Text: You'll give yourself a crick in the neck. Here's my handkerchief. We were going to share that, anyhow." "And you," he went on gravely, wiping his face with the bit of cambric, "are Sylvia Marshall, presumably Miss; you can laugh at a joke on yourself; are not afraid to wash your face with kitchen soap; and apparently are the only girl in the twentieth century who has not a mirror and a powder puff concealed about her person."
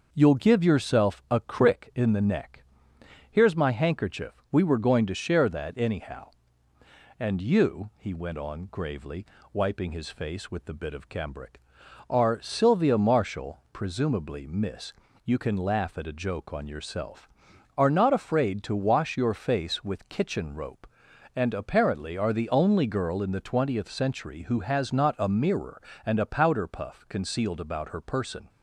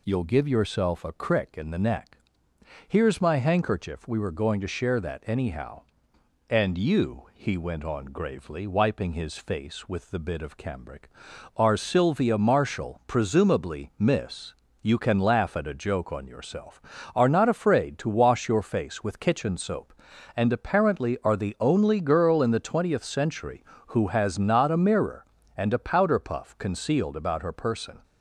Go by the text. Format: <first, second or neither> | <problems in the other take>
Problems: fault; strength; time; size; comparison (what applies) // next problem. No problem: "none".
second | starts louder than the rest; noticeable; until 1.1 s; 6 dB // says "rope" for "soap"; at 20.5 s